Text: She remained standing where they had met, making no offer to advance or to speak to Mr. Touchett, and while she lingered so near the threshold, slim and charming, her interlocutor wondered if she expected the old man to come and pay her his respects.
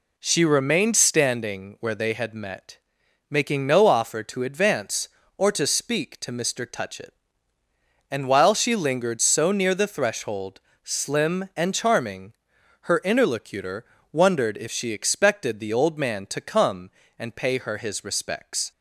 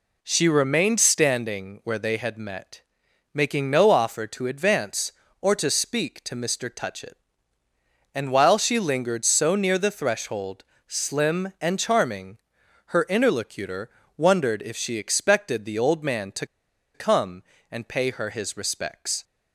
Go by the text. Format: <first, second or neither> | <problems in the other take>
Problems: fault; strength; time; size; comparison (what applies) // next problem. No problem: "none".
first | pauses between "interlocutor" and "wondered"; slight; at 13.8 s; 0.28 s long; slight in the first // pauses between "to" and "come"; noticeable; at 16.4 s; 0.49 s long